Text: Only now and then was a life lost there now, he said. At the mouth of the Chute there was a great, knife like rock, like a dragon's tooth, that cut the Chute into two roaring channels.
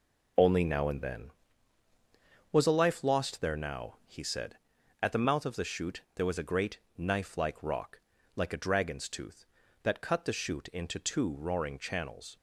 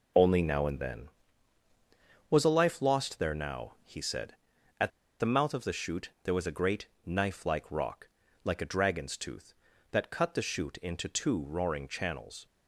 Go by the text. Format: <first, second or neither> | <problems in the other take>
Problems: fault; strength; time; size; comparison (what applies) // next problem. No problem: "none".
first | pauses between "At" and "the"; slight; at 4.8 s; 0.30 s long